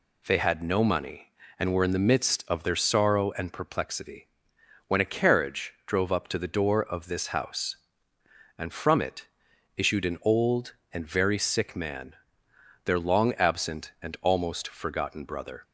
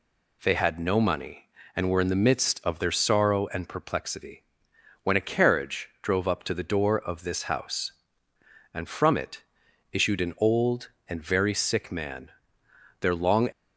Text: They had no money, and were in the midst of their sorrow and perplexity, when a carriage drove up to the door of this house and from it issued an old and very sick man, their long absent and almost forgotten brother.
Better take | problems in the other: first | pauses between "it" and "issued"; noticeable; at 9.4 s; 0.50 s long; noticeable in the first // stops before "absent and almost forgotten brother"; at 13.5 s

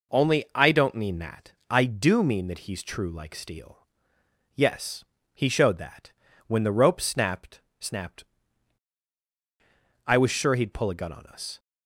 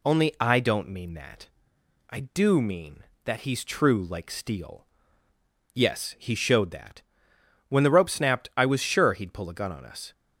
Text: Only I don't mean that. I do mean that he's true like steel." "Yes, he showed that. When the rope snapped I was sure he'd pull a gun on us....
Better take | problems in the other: second | says "snapped" twice; at 7.7 s

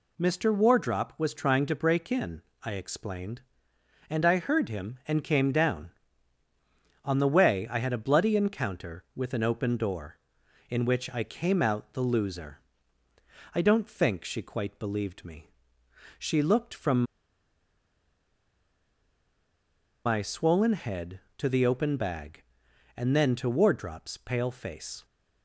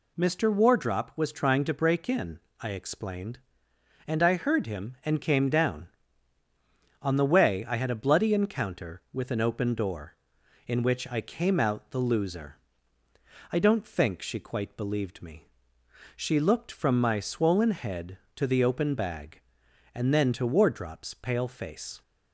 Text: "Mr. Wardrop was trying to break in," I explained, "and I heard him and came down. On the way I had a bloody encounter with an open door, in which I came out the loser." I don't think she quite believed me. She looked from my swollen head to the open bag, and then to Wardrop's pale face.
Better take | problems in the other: second | pauses between "from" and "my"; strong; at 17.0 s; 3.0 s long

